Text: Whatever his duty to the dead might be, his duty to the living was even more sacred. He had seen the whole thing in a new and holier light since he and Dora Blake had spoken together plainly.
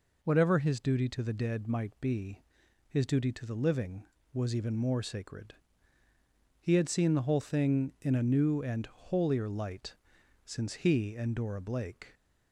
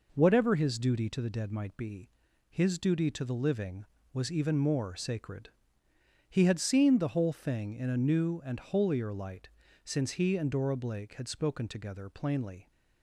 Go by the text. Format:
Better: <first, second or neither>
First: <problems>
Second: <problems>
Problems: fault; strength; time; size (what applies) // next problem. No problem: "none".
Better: second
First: pauses between "light" and "since"; noticeable; at 9.9 s; 0.50 s long // stops before "had spoken together plainly"; at 12.1 s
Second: pauses between "light" and "since"; slight; at 9.4 s; 0.36 s long